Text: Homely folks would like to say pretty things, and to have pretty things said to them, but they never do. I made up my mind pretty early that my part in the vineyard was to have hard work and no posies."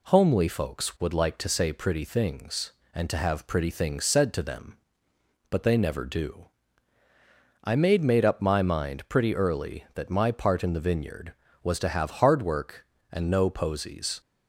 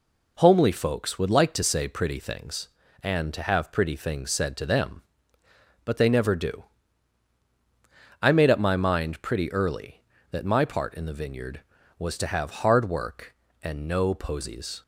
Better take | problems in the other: second | says "made" twice; at 8.0 s

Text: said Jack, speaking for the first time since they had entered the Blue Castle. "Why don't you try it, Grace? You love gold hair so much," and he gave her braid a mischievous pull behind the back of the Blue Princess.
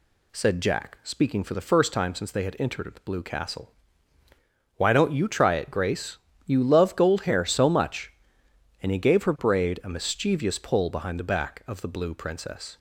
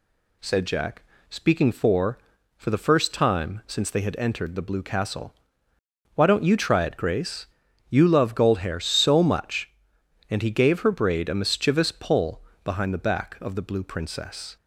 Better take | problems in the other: first | says "for" twice; at 2.5 s // pauses between "pull" and "behind"; slight; at 12.4 s; 0.22 s long

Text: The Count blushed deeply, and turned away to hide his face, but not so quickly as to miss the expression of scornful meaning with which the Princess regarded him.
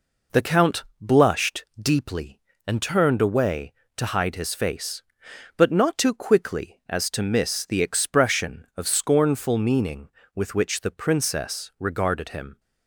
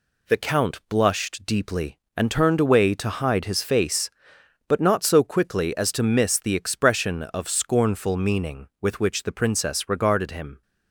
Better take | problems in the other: second | pauses between "Count" and "blushed"; slight; at 0.8 s; 0.16 s long // pauses between "blushed" and "deeply"; slight; at 1.6 s; 0.16 s long // says "too" for "so"; at 5.9 s

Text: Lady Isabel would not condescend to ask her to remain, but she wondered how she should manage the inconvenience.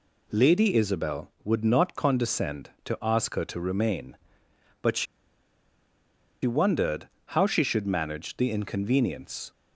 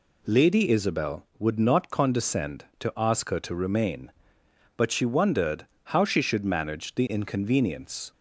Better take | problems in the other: second | pauses between "she" and "wondered"; strong; at 5.0 s; 1.3 s long // pauses between "wondered" and "how"; slight; at 7.0 s; 0.22 s long; slight in the second

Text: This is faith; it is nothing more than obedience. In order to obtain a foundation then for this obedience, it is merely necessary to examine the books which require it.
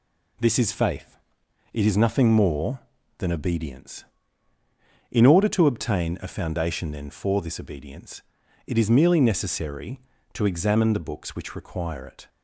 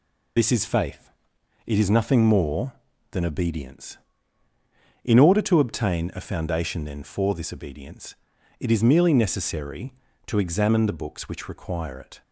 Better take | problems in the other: first | loses the start of "This"; at 0.3 s; 55 ms

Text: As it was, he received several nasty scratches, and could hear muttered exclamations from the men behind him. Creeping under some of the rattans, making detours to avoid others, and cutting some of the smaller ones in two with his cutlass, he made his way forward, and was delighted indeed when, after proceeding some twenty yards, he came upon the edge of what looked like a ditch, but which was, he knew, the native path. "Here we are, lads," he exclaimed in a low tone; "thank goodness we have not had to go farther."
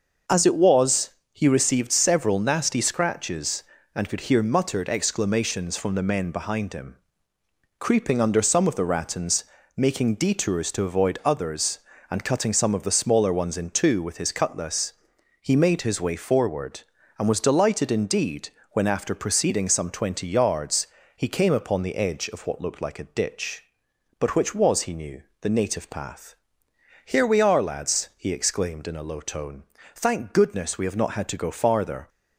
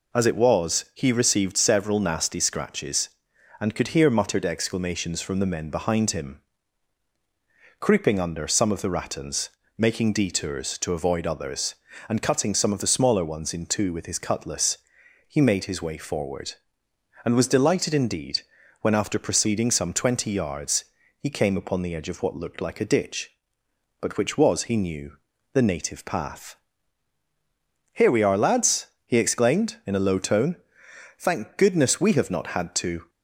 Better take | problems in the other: first | pauses between "indeed" and "when"; at 18.4 s; 0.40 s long; slight in the first // stops before "go farther"; at 33.0 s

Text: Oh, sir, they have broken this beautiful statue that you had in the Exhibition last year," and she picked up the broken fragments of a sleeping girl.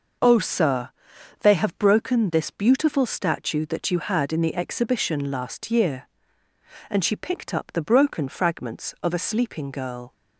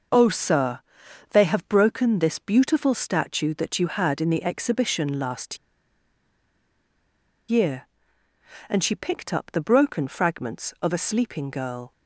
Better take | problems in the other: first | pauses between "last" and "year"; strong; at 5.5 s; 1.9 s long

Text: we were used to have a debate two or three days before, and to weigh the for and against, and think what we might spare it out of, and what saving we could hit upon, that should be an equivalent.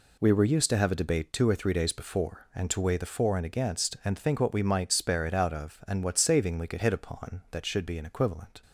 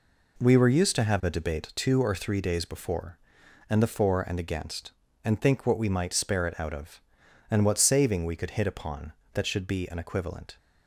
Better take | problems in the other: first | skips "to weigh"; at 3.8 s

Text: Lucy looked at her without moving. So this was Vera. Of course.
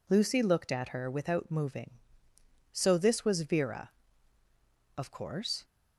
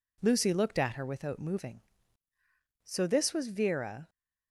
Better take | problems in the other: first | stops before "Of course"; at 4.0 s

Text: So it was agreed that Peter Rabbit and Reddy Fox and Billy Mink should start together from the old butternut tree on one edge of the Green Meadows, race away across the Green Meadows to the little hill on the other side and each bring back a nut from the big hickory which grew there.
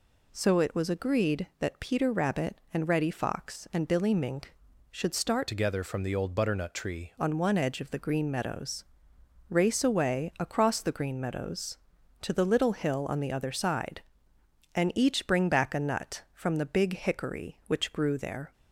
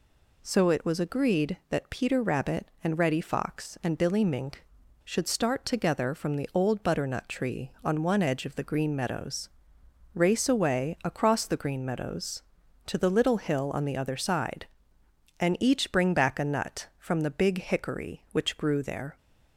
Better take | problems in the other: second | changes voice from "together" to "tree"; from 5.4 to 7.1 s; 1.7 s long

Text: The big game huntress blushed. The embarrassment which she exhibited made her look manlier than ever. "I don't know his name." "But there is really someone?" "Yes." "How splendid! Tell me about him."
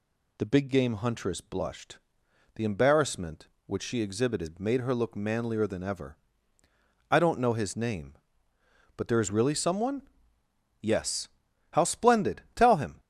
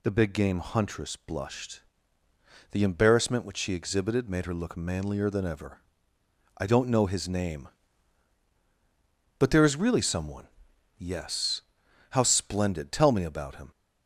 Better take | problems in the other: second | skips "me about"; at 12.7 s

